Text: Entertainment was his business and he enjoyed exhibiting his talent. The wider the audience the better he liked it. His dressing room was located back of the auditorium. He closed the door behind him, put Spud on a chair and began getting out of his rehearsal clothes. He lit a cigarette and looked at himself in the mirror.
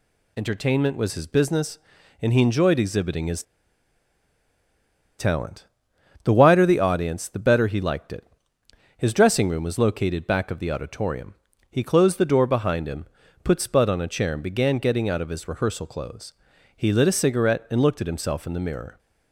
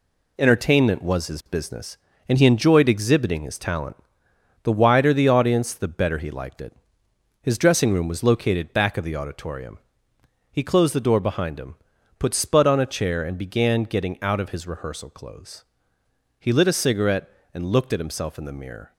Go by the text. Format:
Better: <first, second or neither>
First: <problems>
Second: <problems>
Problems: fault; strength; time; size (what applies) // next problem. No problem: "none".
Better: second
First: pauses between "his" and "talent"; strong; at 3.4 s; 1.7 s long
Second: none